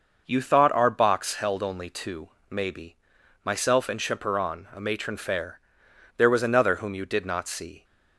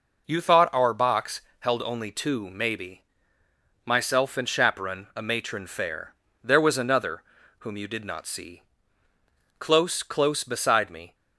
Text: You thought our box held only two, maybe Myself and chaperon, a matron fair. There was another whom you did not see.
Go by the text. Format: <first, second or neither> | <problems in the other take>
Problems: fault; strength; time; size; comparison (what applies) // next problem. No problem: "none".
first | pauses between "box" and "held"; slight; at 1.4 s; 0.18 s long // pauses between "maybe" and "Myself"; noticeable; at 3.0 s; 0.82 s long; noticeable in the first // pauses between "another" and "whom"; at 7.2 s; 0.38 s long // goes on to say "Close close beside me"; from 9.5 s on; 1.5 s long